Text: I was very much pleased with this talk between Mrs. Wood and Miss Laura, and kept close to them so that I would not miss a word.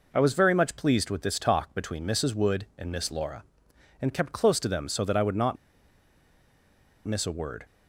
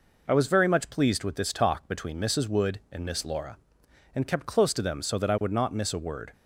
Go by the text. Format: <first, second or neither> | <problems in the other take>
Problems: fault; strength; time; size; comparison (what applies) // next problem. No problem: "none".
second | pauses between "not" and "miss"; strong; at 5.5 s; 1.5 s long